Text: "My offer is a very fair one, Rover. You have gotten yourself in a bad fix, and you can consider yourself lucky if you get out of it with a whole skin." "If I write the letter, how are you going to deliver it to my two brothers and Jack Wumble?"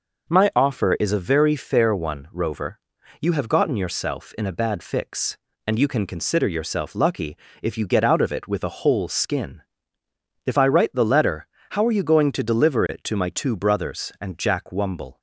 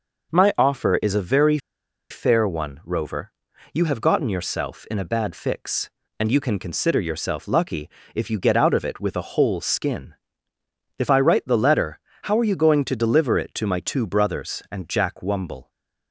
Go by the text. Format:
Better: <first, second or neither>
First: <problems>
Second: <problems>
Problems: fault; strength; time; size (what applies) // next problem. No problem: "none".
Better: first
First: pauses between "lucky" and "if"; slight; at 7.3 s; 0.26 s long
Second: pauses between "very" and "fair"; noticeable; at 1.5 s; 0.53 s long // pauses between "lucky" and "if"; slight; at 7.8 s; 0.26 s long